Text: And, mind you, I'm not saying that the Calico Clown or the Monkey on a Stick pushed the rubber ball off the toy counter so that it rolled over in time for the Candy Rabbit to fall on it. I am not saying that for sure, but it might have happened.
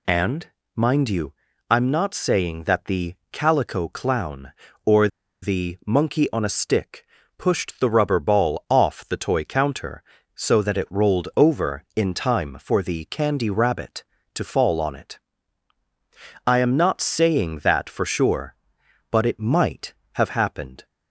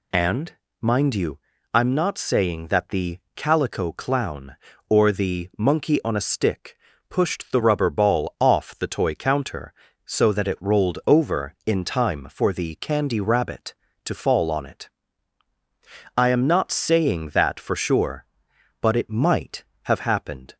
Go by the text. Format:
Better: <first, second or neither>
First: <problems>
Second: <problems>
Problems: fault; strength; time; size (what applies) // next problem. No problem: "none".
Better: second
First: pauses between "the" and "Calico"; slight; at 3.1 s; 0.16 s long // pauses between "or" and "the"; slight; at 5.0 s; 0.35 s long // pauses between "Stick" and "pushed"; slight; at 7.0 s; 0.32 s long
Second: pauses between "the" and "Calico"; slight; at 3.1 s; 0.16 s long // pauses between "Stick" and "pushed"; slight; at 6.7 s; 0.32 s long